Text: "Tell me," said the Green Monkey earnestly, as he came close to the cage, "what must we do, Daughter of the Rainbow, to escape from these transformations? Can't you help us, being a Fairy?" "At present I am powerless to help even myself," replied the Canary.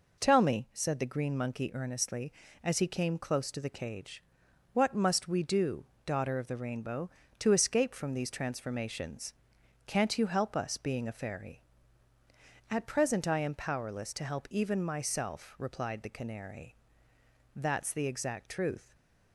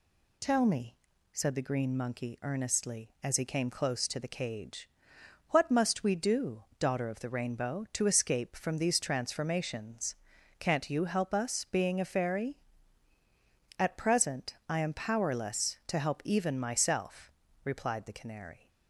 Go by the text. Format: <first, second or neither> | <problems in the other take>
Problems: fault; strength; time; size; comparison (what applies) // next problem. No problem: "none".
second | goes on to say "That's the exact truth"; from 17.5 s on; 1.4 s long // stays silent after the last word; slight; from 18.8 s on; 0.5 s long